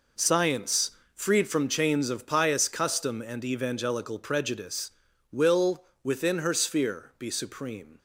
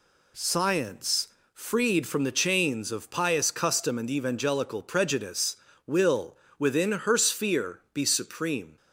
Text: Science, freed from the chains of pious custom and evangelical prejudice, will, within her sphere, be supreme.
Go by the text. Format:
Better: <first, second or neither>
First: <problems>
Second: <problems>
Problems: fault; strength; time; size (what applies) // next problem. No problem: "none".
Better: second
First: skips "the"; at 1.6 s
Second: none